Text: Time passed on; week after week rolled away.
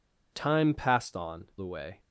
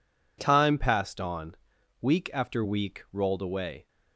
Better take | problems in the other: second | skips "week after week rolled"; at 1.5 s

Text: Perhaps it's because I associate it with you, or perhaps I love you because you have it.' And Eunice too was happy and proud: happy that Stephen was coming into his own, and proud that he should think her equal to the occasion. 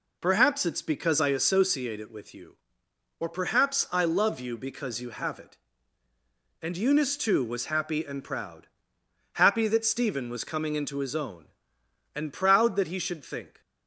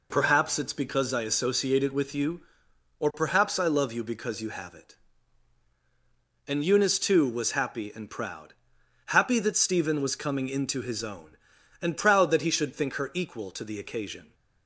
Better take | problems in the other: second | stops before "her equal to the occasion"; at 13.6 s

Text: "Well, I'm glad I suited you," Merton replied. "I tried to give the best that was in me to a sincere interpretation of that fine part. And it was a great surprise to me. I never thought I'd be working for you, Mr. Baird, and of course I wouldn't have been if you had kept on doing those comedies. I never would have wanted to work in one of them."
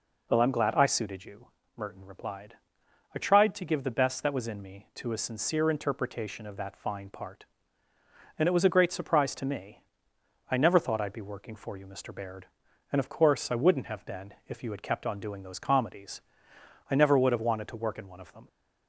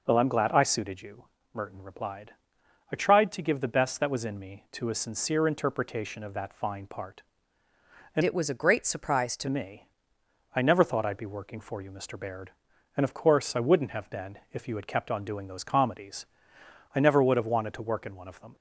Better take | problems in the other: first | changes voice from "it" to "to"; from 8.2 to 9.4 s; 1.2 s long // pauses between "been" and "if"; slight; at 14.3 s; 0.16 s long; slight in the first

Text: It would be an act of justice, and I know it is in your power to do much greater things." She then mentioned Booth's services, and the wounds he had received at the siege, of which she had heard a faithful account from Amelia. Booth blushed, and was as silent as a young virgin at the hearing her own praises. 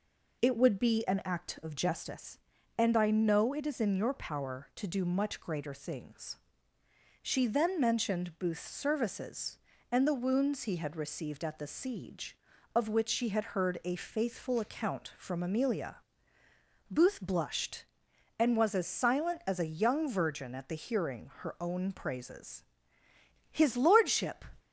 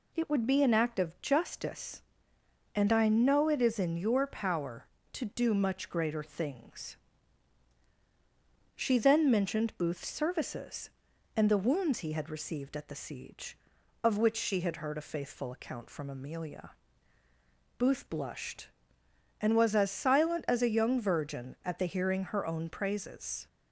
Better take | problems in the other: second | goes on to say "His lordship"; noticeable; from 23.5 s on; 0.94 s long

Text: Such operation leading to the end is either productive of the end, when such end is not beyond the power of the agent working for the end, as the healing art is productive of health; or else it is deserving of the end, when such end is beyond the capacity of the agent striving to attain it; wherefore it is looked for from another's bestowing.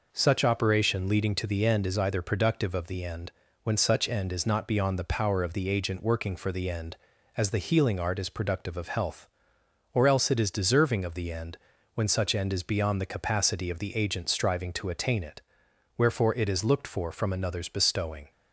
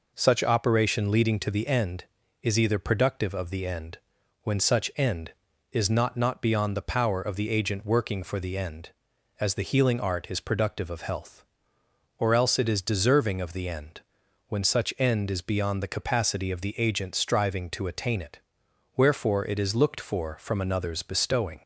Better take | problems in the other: first | says "not" twice; at 6.1 s

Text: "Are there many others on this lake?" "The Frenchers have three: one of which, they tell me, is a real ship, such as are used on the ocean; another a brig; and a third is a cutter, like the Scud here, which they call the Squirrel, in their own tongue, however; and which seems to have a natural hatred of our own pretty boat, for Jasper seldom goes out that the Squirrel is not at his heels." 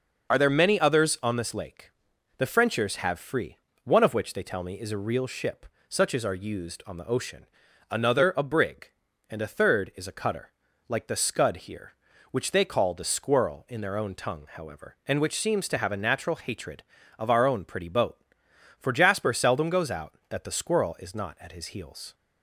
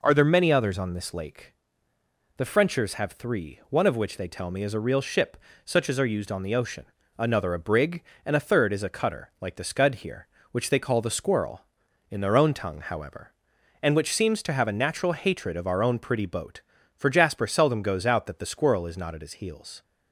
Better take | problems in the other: second | starts louder than the rest; until 1.3 s; 6 dB // says "free" for "three"; at 3.1 s

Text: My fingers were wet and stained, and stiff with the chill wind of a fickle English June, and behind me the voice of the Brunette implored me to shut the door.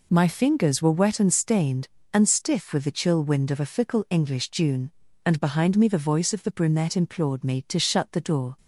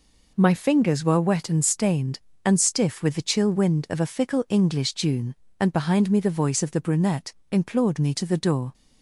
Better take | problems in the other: first | pauses between "Brunette" and "implored"; slight; at 7.3 s; 0.18 s long // skips "shut"; at 8.2 s

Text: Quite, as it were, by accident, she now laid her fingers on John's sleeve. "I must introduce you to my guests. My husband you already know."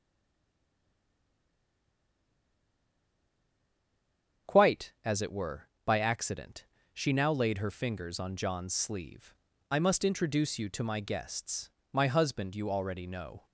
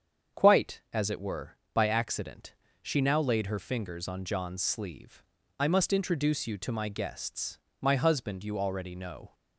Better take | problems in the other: second | stays silent before the first word; strong; until 4.4 s; 4.4 s long // starts louder than the rest; strong; until 5.5 s; 7.5 dB; strong in the second

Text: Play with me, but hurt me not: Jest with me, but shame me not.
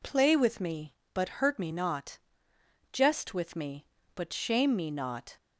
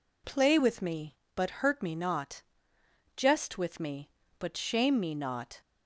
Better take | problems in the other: neither | none

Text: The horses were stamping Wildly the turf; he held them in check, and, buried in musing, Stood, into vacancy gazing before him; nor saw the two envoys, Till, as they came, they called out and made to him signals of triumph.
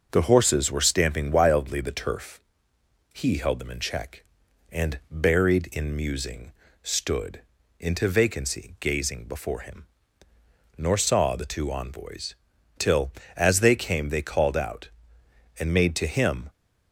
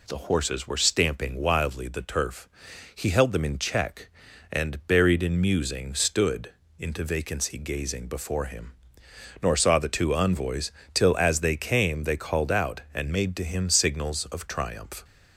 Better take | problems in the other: second | starts louder than the rest; until 1.1 s; 6.5 dB // stops before "signals of triumph"; at 16.4 s

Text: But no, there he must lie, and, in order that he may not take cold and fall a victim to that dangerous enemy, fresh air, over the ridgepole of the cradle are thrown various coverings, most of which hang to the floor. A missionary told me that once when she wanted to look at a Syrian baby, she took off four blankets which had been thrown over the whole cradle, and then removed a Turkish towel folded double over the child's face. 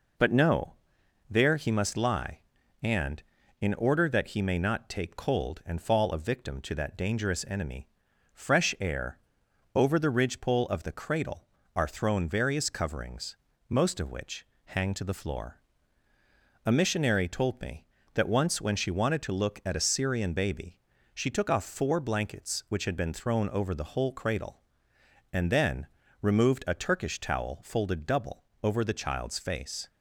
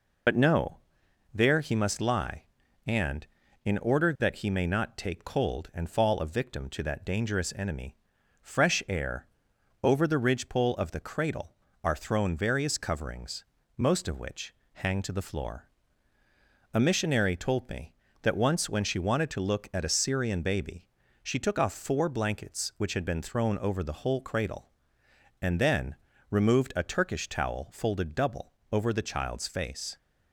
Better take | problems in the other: first | loses the start of "But"; at 0.2 s; 55 ms // pauses between "which" and "hang"; slight; at 14.5 s; 0.20 s long; slight in the first // pauses between "then" and "removed"; slight; at 25.9 s; 0.36 s long; slight in the first // pauses between "double" and "over"; slight; at 28.5 s; 0.18 s long; slight in the first

